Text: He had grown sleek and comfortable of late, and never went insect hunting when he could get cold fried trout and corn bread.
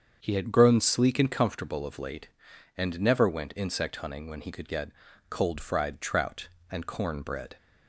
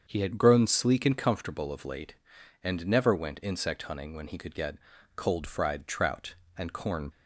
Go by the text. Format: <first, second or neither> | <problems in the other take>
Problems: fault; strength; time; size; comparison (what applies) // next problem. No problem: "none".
first | starts louder than the rest; until 1.0 s; 7 dB; strong in the first // pauses between "get" and "cold"; at 4.7 s; 0.40 s long; also in the first // stops before "bread"; at 7.1 s